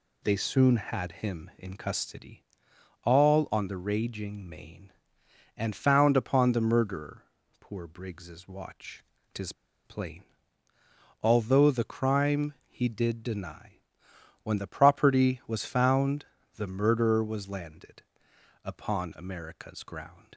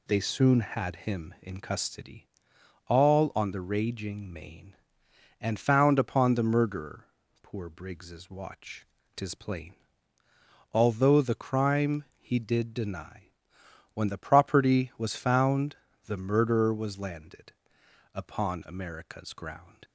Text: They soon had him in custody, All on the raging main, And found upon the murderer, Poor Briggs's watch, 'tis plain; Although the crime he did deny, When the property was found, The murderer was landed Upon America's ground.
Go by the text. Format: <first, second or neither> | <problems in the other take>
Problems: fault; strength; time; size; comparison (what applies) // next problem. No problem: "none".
second | pauses between "tis" and "plain"; slight; at 9.5 s; 0.33 s long // pauses between "landed" and "Upon"; noticeable; at 18.0 s; 0.62 s long; noticeable in the second